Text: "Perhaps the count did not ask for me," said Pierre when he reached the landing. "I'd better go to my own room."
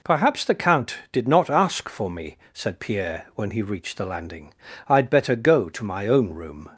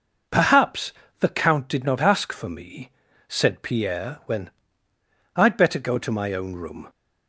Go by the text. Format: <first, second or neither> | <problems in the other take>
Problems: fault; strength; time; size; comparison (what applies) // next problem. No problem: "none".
first | pauses between "Perhaps" and "the"; slight; at 0.9 s; 0.30 s long // skips "he reached the landing"; at 4.9 s